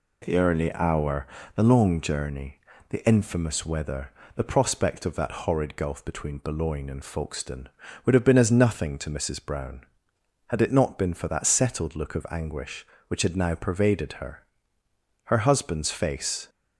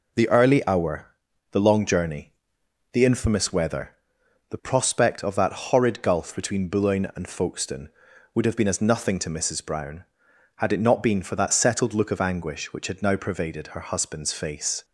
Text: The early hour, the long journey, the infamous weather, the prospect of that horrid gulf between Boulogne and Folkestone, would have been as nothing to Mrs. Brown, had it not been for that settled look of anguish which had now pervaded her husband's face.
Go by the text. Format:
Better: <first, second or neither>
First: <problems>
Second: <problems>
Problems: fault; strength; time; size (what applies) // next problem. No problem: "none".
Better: second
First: says "her" twice; at 15.2 s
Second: none